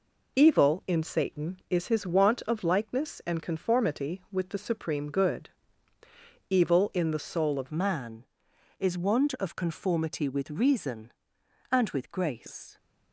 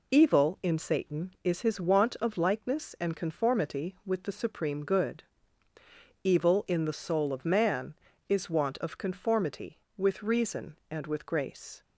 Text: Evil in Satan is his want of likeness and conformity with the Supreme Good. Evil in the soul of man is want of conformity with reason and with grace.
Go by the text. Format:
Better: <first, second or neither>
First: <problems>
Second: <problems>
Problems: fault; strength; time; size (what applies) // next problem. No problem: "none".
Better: second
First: changes voice at "man"; from 7.7 s on; 5.0 s long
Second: none